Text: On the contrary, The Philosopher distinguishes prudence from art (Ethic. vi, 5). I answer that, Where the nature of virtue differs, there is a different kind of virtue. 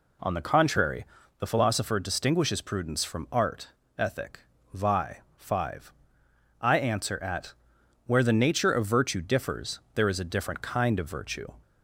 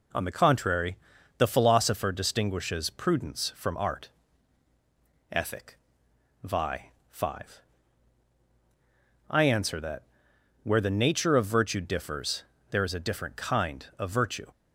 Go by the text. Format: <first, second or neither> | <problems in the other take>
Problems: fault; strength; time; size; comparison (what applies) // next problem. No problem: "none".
second | says "at" for "that"; at 7.2 s